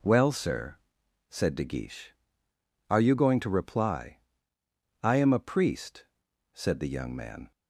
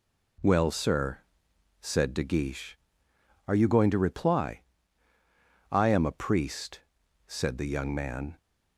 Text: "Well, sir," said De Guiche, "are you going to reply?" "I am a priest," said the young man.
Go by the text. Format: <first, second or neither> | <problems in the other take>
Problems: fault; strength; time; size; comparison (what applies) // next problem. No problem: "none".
neither | none